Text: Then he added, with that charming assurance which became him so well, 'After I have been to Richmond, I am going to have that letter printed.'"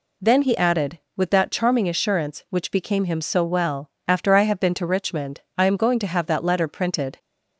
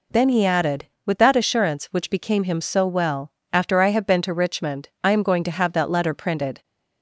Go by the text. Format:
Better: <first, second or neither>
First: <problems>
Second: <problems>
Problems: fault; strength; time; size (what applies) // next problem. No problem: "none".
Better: first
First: none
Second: skips "charming"; at 1.3 s